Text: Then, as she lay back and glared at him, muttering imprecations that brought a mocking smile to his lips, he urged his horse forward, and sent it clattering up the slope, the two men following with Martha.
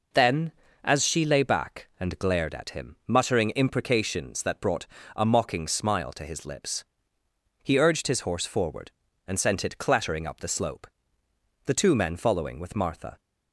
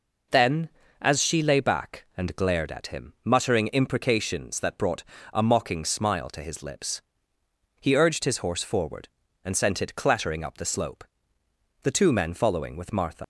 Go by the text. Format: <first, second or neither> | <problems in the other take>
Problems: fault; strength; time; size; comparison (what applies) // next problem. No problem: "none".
first | pauses between "brought" and "a"; slight; at 5.0 s; 0.28 s long; slight in the first // leaves "Martha" unfinished; at 13.2 s; 115 ms